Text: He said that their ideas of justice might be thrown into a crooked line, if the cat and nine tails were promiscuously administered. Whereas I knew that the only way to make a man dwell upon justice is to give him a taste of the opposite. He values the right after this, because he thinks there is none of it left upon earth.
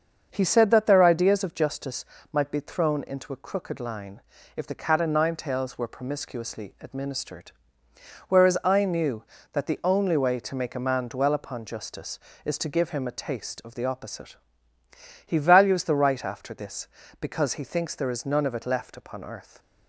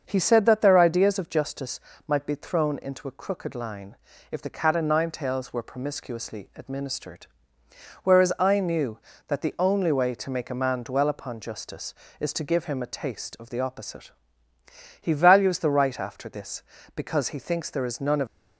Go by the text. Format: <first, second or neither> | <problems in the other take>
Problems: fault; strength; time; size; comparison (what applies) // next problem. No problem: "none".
first | starts louder than the rest; until 1.0 s; 6.5 dB; also in the first // pauses between "justice" and "might"; slight; at 1.7 s; 0.26 s long; slight in the first // stops before "it left upon earth"; at 18.2 s